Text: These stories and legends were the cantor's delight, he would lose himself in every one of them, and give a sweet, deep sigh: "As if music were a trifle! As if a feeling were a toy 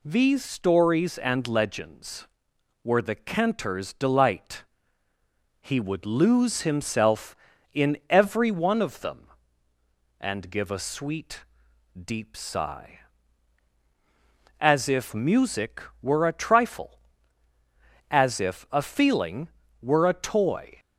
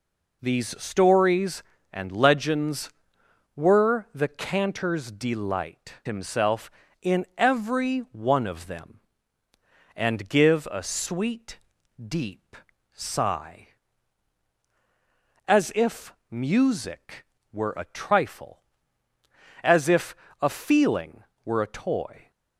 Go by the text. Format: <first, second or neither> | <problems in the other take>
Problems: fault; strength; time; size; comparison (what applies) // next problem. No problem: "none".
first | skips "he would lose"; at 6.0 s // pauses between "deep" and "sigh"; slight; at 12.5 s; 0.36 s long // pauses between "if" and "music"; slight; at 16.1 s; 0.16 s long // pauses between "if" and "a"; slight; at 20.1 s; 0.24 s long